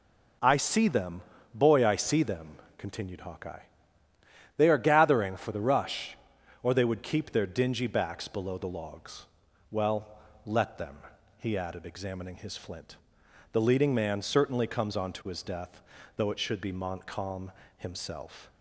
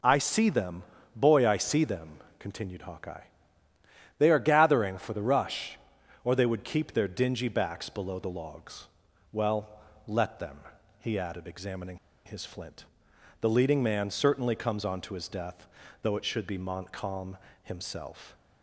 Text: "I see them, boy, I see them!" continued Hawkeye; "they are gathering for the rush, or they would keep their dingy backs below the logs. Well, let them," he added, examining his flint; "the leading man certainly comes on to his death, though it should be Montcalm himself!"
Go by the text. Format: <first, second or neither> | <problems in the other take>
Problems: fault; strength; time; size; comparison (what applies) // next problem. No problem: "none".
first | pauses between "examining" and "his"; slight; at 11.9 s; 0.27 s long // pauses between "Montcalm" and "himself"; slight; at 17.3 s; 0.26 s long; slight in the first